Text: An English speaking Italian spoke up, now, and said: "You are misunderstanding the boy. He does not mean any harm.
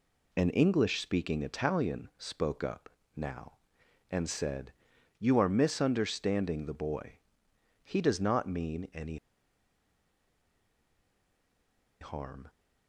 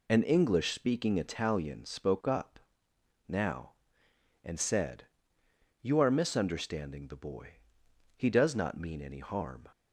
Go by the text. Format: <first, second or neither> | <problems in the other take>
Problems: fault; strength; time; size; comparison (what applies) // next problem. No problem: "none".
second | pauses between "any" and "harm"; strong; at 9.1 s; 2.8 s long